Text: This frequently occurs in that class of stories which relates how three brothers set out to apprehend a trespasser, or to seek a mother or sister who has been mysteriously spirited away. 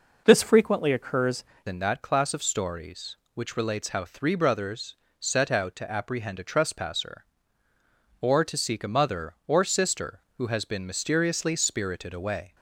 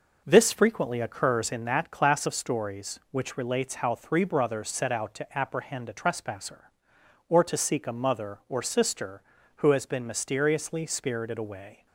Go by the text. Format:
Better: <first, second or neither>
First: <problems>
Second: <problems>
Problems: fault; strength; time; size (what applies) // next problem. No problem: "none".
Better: second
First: changes voice at "in"; from 1.6 s on; 10.9 s long // pauses between "brothers" and "set"; slight; at 4.9 s; 0.24 s long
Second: none